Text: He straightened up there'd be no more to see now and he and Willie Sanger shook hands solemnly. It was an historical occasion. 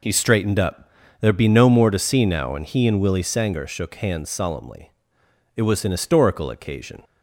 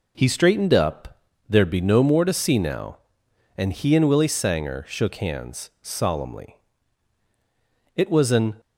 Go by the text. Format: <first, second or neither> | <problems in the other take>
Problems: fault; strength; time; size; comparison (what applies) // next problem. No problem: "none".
first | pauses between "up" and "there'd"; slight; at 1.1 s; 0.28 s long; slight in the first // stops before "historical occasion"; at 8.5 s